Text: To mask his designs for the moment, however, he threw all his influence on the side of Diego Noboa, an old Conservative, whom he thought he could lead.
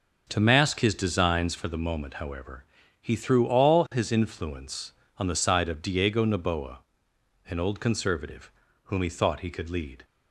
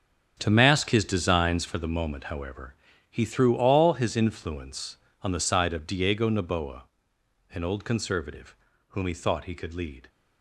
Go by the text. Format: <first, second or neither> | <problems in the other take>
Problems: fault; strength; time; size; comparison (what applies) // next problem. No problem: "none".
first | gets quieter; strong; throughout; 12 dB